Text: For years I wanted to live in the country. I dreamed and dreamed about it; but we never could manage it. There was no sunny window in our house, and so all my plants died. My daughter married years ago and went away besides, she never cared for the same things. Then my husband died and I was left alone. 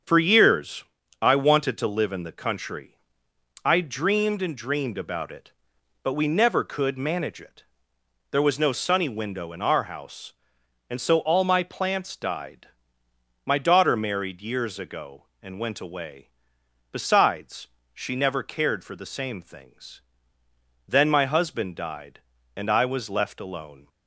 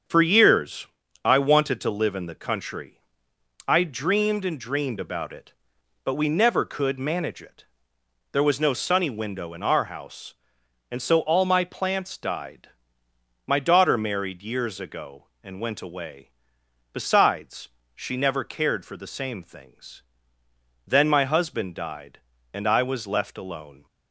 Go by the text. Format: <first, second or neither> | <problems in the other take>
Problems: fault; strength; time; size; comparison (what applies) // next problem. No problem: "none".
neither | starts louder than the rest; strong; the same in both // pauses between "years" and "I"; the same in both // pauses between "away" and "besides"; noticeable; the same in both